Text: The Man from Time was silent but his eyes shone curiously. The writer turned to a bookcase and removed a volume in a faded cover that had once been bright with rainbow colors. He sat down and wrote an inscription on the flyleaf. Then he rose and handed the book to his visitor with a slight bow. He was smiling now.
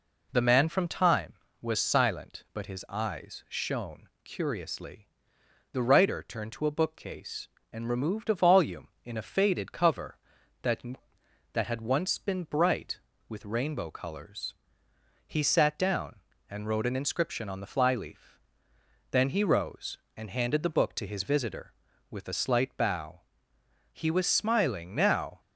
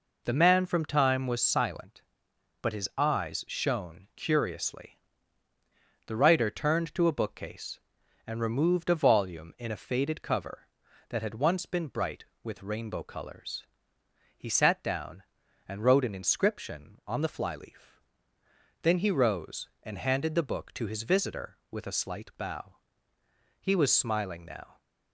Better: second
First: pauses between "shone" and "curiously"; slight; at 4.0 s; 0.18 s long // says "that" twice; at 11.5 s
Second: none

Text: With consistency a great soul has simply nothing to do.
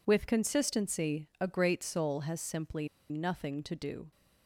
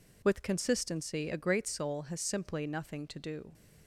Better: second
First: pauses between "simply" and "nothing"; slight; at 2.8 s; 0.22 s long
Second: none

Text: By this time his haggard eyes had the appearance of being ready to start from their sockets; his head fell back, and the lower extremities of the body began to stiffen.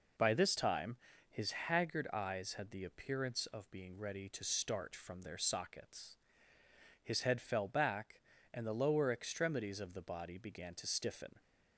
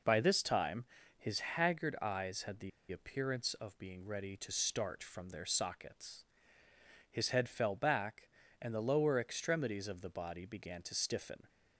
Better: first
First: pauses between "time" and "his"; slight; at 0.9 s; 0.32 s long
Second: pauses between "time" and "his"; slight; at 0.8 s; 0.32 s long // pauses between "the" and "appearance"; slight; at 2.7 s; 0.21 s long

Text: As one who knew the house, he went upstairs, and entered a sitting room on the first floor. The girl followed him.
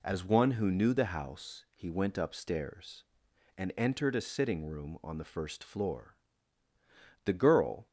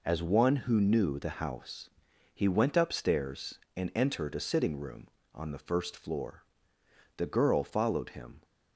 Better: second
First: stops before "followed him"; at 7.8 s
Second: none

